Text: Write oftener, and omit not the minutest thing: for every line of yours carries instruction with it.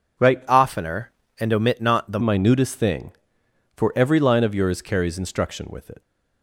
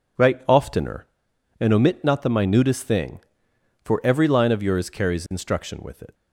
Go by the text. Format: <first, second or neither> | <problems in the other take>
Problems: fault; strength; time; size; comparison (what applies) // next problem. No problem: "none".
second | changes voice from "oftener" to "the"; from 0.4 to 2.1 s; 1.7 s long